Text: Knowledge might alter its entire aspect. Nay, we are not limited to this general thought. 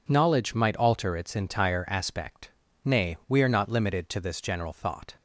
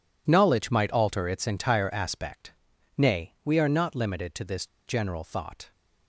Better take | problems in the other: first | pauses between "this" and "general"; slight; at 4.6 s; 0.20 s long

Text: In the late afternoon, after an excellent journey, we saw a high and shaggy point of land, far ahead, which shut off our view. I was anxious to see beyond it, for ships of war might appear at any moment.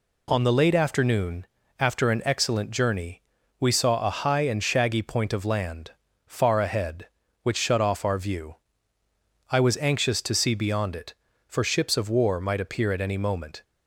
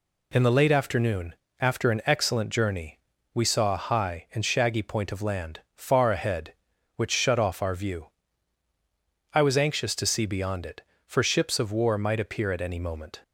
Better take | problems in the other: second | says "On" for "In"; at 0.2 s

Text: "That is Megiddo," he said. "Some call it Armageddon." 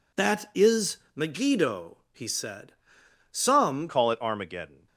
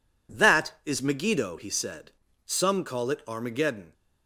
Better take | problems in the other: second | pauses between "is" and "Megiddo"; slight; at 0.9 s; 0.16 s long // changes voice at "call"; from 3.8 s on; 1.0 s long

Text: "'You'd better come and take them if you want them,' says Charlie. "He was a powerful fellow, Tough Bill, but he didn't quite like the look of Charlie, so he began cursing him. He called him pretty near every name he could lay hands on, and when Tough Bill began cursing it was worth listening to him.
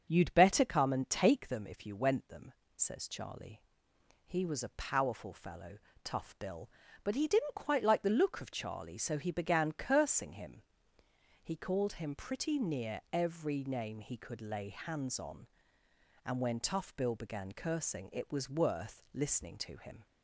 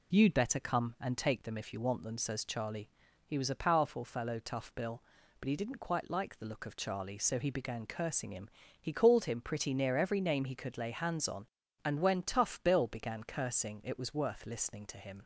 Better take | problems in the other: second | starts louder than the rest; until 1.1 s; 6.5 dB // says "went" for "want"; at 1.9 s

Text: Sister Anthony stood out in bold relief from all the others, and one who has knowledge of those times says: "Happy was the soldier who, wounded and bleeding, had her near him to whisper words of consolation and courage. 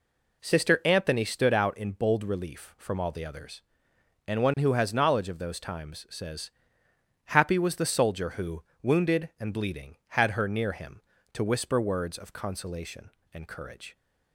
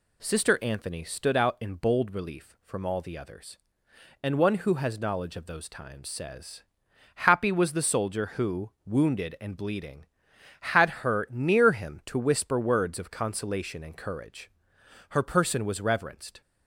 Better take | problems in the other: first | pauses between "had" and "her"; slight; at 10.8 s; 0.18 s long // goes on to say "Her person was reverenced"; from 15.0 s on; 1.3 s long

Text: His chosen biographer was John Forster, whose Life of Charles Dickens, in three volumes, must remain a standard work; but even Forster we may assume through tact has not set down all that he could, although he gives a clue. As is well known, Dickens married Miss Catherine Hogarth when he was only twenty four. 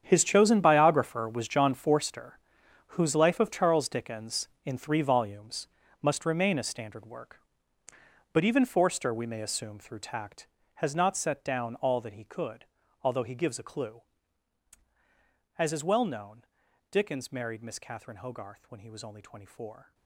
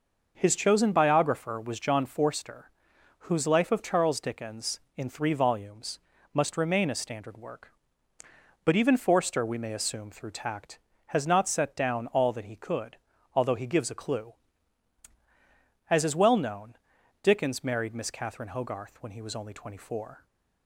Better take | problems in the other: second | gets quieter; strong; throughout; 15 dB

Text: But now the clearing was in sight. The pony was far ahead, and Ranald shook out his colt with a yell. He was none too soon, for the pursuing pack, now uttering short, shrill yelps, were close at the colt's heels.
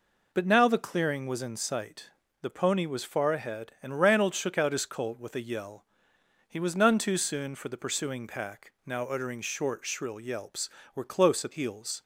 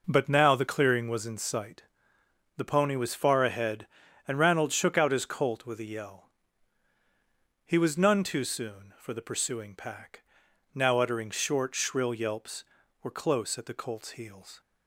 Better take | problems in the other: second | skips "the colt's"; at 11.5 s

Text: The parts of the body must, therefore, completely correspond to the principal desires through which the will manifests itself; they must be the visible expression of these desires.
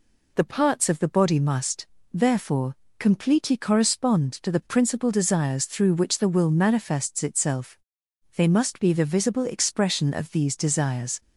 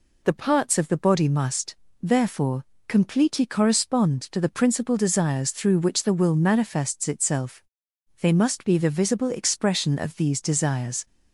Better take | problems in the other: neither | none

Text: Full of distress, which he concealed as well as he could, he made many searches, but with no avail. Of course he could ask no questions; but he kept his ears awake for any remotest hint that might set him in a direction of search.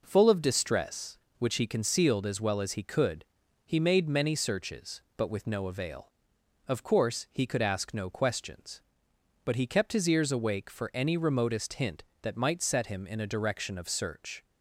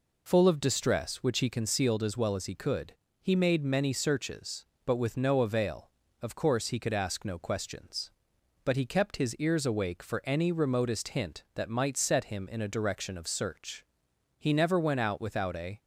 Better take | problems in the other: first | goes on to say "He never went out without a"; from 14.3 s on; 1.4 s long

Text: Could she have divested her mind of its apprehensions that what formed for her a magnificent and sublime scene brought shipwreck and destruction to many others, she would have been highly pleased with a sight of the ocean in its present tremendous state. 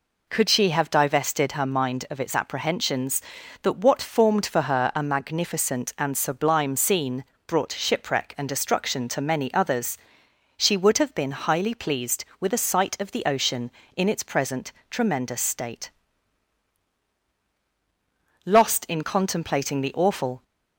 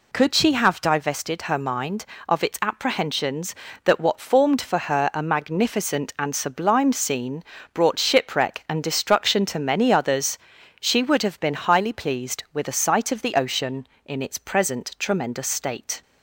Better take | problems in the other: second | pauses between "scene" and "brought"; slight; at 7.2 s; 0.24 s long; slight in the second // pauses between "present" and "tremendous"; slight; at 14.7 s; 0.18 s long // goes on to say "Lost in contemplating the awful"; strong; from 18.4 s on; 1.9 s long

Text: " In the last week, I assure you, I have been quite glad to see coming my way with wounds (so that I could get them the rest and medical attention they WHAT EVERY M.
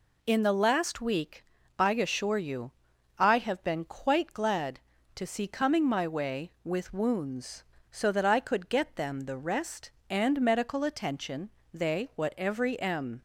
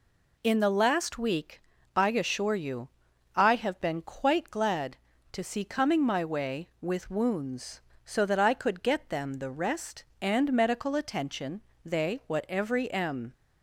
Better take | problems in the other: neither | pauses between "attention" and "they"; slight; the same in both

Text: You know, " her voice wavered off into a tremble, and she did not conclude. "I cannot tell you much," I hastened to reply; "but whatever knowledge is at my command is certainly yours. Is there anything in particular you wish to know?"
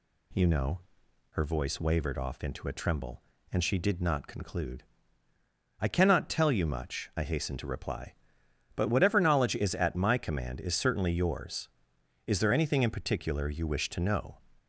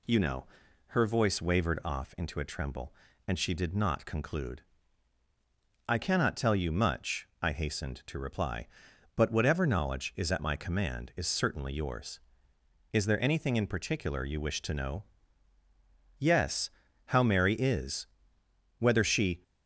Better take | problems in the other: first | goes on to say "Yes how Mary is whether she"; strong; from 16.1 s on; 3.2 s long

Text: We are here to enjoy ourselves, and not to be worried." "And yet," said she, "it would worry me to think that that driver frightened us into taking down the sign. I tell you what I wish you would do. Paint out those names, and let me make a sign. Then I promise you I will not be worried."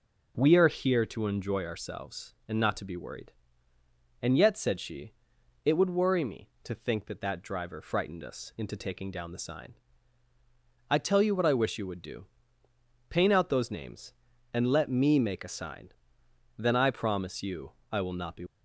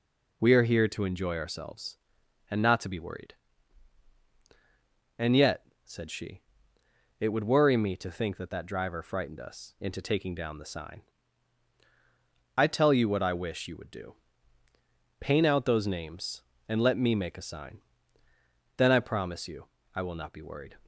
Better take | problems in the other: second | pauses between "you" and "I"; slight; at 17.7 s; 0.18 s long; slight in the second // stops before "worried"; at 18.4 s

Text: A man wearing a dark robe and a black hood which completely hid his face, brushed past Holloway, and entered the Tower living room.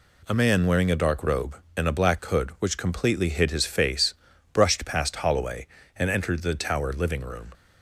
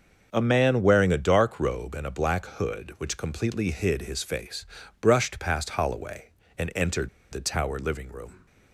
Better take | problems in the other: first | starts louder than the rest; until 1.3 s; 6.5 dB // pauses between "entered" and "the"; slight; at 7.0 s; 0.24 s long

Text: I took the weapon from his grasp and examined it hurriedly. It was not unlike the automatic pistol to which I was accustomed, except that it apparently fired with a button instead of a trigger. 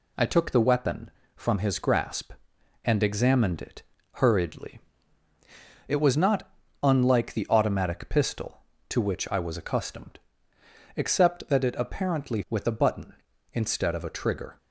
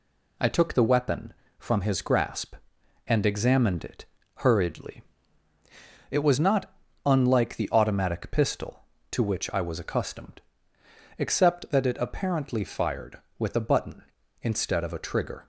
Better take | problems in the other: second | pauses between "it" and "hurriedly"; slight; at 3.8 s; 0.30 s long; slight in the second // pauses between "not" and "unlike"; slight; at 6.4 s; 0.36 s long; slight in the second // skips "fired"; at 12.4 s

